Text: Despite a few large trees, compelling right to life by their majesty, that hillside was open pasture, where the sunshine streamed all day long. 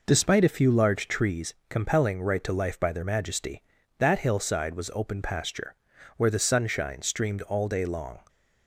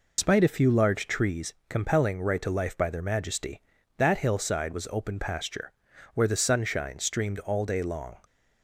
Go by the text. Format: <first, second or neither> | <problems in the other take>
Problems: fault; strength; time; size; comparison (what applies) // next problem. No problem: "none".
first | loses the start of "Despite"; at 0.1 s; 115 ms